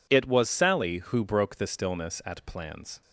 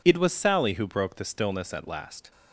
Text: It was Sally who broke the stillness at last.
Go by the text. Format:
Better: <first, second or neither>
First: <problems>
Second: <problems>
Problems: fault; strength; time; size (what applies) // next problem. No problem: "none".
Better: second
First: says "plans" for "last"; at 2.4 s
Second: none